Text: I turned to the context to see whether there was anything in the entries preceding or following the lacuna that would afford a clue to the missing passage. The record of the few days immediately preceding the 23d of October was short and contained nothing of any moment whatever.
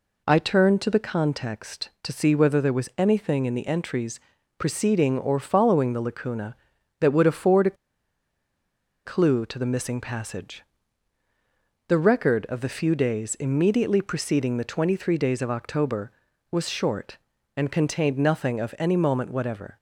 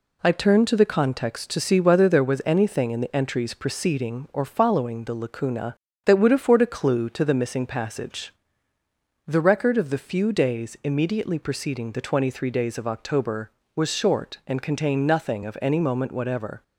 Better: second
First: pauses between "entries" and "preceding"; at 4.1 s; 0.38 s long // pauses between "a" and "clue"; strong; at 7.7 s; 1.3 s long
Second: none

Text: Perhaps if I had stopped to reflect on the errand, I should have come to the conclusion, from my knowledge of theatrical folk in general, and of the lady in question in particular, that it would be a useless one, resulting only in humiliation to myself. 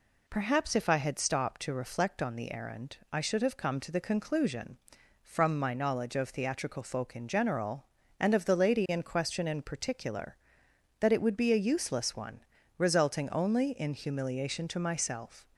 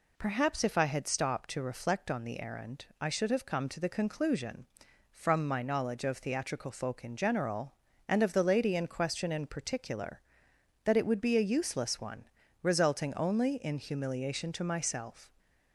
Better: neither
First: none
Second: none

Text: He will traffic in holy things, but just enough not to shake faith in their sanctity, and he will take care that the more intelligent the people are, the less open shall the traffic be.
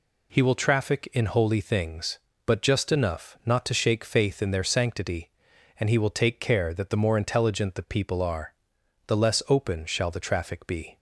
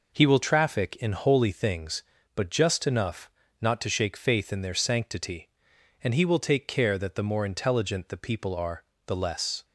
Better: first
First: none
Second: pauses between "enough" and "not"; slight; at 3.3 s; 0.28 s long // stops before "open shall the traffic be"; at 9.6 s

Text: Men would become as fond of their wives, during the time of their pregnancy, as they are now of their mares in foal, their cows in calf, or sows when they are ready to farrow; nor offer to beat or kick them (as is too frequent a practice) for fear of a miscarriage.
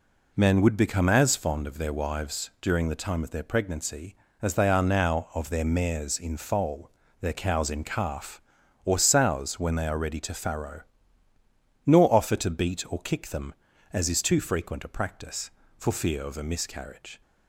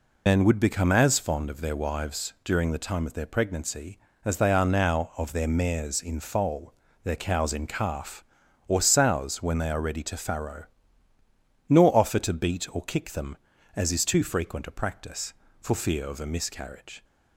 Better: first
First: none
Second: loses the start of "Men"; at 0.2 s; 85 ms

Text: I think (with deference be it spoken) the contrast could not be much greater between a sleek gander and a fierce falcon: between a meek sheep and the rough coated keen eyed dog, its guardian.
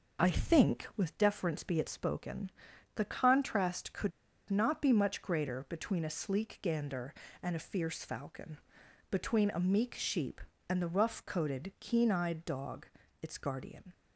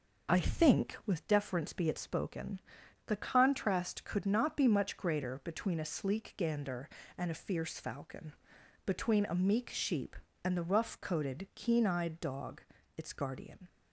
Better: second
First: pauses between "could" and "not"; at 4.1 s; 0.37 s long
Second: none

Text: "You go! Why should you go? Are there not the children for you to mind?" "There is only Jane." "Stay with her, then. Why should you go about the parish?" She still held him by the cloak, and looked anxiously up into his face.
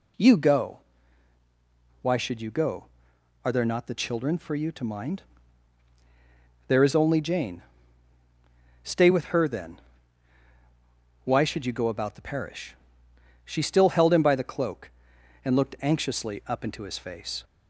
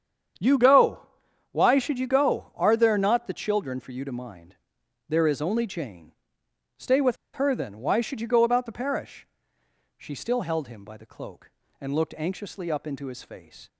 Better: first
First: none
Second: starts louder than the rest; strong; until 1.8 s; 8 dB // pauses between "with" and "her"; slight; at 7.1 s; 0.17 s long

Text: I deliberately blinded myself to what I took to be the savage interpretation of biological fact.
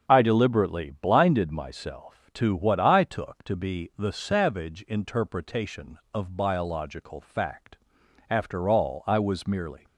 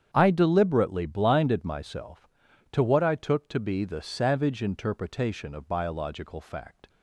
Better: second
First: starts louder than the rest; strong; until 1.0 s; 7 dB // goes on to say "After all I was merely"; from 8.2 s on; 1.5 s long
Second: starts louder than the rest; strong; until 1.1 s; 8.5 dB

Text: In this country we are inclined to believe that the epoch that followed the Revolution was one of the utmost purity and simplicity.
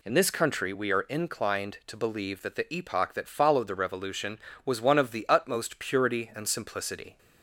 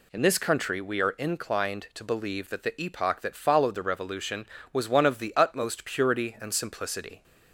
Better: neither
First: none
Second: none

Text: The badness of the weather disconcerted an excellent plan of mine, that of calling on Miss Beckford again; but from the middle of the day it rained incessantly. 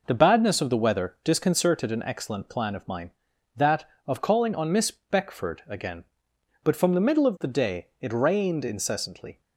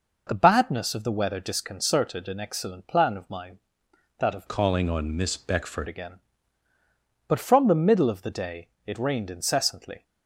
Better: first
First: none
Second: changes voice from "calling" to "Beckford"; from 4.4 to 5.8 s; 1.4 s long // pauses between "day" and "it"; slight; at 8.6 s; 0.18 s long

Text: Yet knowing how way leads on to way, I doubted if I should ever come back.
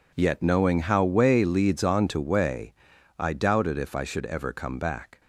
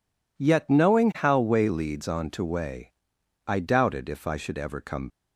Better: first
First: none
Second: stops before "back"; at 5.0 s

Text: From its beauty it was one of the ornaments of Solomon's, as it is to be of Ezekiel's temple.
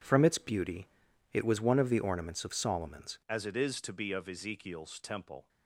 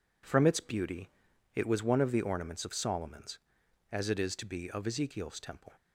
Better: second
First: pauses between "beauty" and "it"; at 0.8 s; 0.44 s long // changes voice at "as"; from 3.2 s on; 2.2 s long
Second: pauses between "beauty" and "it"; at 1.1 s; 0.44 s long

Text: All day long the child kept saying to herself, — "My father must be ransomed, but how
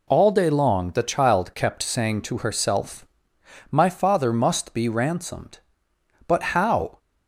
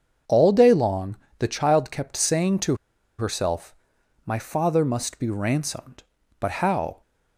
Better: first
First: none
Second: starts louder than the rest; until 1.5 s; 7 dB // pauses between "long" and "the"; slight; at 1.1 s; 0.22 s long // pauses between "to" and "herself"; at 2.7 s; 0.43 s long

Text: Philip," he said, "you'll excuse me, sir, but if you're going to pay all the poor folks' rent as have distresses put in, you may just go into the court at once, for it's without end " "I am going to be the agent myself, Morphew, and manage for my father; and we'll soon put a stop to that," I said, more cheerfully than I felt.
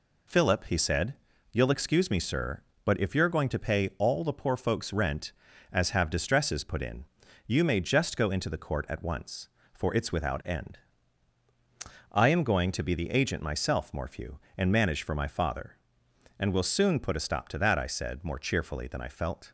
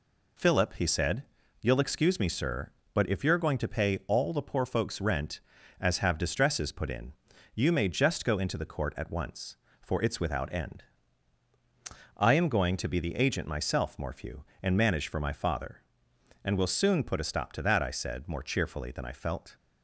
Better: neither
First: none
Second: none

